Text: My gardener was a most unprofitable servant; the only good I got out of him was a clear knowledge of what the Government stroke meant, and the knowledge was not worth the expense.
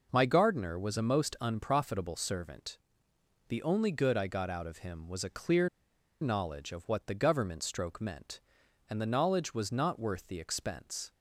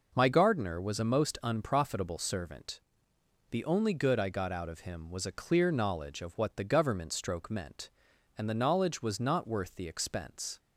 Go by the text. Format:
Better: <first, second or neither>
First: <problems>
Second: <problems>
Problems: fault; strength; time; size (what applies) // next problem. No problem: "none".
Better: second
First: pauses between "clear" and "knowledge"; noticeable; at 5.6 s; 0.53 s long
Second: none